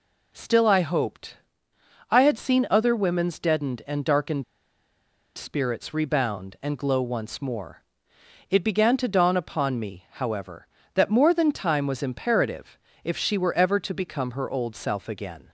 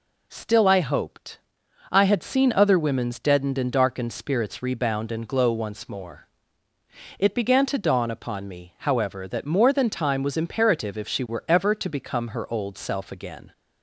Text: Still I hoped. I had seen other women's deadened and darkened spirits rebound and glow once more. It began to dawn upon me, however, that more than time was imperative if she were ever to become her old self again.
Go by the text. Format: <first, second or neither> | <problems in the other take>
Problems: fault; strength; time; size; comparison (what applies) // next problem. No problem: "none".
second | pauses between "darkened" and "spirits"; noticeable; at 4.4 s; 0.92 s long // pauses between "imperative" and "if"; slight; at 12.7 s; 0.26 s long